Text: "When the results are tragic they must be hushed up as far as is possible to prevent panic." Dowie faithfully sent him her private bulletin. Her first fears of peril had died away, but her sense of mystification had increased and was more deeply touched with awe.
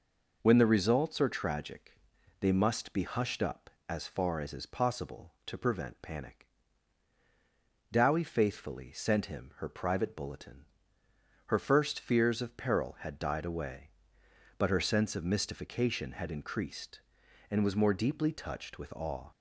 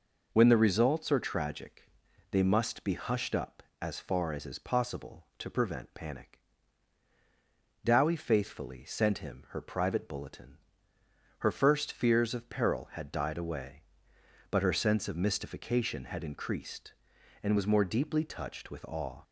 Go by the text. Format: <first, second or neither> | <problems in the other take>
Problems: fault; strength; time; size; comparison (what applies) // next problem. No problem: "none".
neither | pauses between "tragic" and "they"; the same in both